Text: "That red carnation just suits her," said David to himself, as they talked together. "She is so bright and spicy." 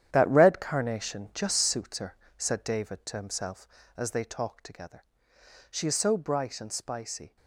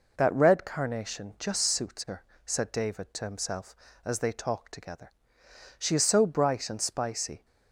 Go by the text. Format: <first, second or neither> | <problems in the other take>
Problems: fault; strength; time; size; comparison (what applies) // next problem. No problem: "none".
second | gets quieter; strong; throughout; 11 dB